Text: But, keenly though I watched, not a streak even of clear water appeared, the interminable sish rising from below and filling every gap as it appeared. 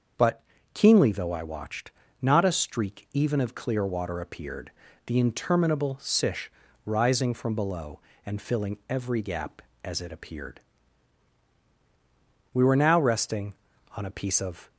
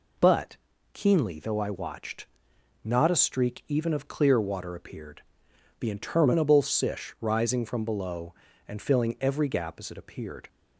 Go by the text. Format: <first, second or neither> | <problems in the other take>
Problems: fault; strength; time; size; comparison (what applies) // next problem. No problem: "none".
second | starts louder than the rest; until 1.4 s; 6.5 dB // pauses between "sish" and "rising"; slight; at 6.5 s; 0.34 s long // goes on to say "We were now resting on a piece of"; strong; from 12.5 s on; 2.1 s long